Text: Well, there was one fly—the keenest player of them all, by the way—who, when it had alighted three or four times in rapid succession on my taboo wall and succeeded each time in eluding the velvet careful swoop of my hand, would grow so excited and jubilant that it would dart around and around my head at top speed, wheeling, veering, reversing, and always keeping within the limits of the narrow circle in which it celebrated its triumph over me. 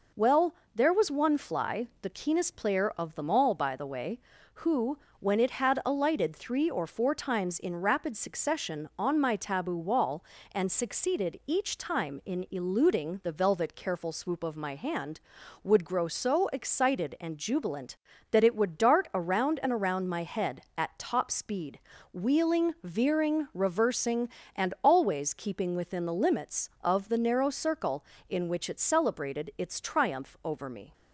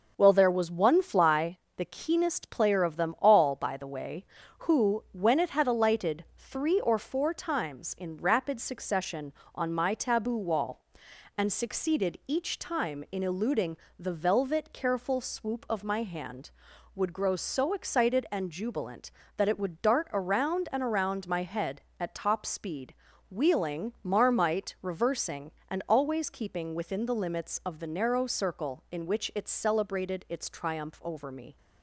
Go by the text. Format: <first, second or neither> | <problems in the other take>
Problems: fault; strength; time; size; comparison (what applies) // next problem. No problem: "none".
first | pauses between "eluding" and "the"; slight; at 13.7 s; 0.24 s long // says "marmite" for "veering"; at 24.0 s